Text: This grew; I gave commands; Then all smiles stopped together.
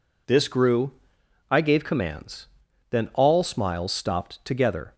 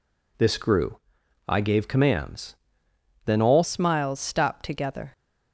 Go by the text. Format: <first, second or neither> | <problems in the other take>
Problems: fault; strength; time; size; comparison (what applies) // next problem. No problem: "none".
first | changes voice at "smiles"; from 3.6 s on; 1.5 s long